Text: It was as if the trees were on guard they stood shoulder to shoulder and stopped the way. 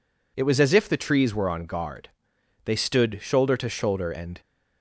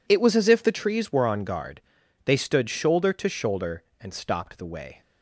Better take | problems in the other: second | pauses between "guard" and "they"; noticeable; at 2.0 s; 0.56 s long; noticeable in the second // stops before "stopped the way"; at 4.4 s

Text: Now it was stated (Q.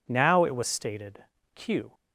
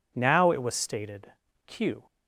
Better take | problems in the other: neither | none

